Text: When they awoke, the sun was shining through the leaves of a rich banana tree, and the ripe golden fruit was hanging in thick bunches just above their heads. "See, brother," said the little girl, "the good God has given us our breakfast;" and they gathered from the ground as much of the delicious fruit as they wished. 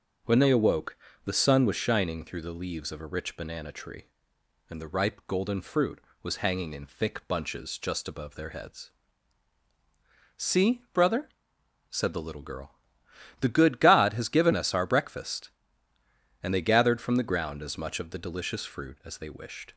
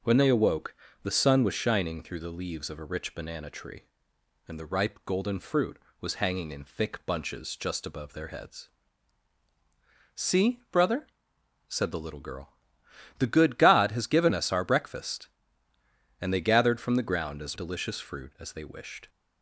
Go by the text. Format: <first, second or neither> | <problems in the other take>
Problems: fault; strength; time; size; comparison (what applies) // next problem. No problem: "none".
first | skips "much of the"; at 17.5 s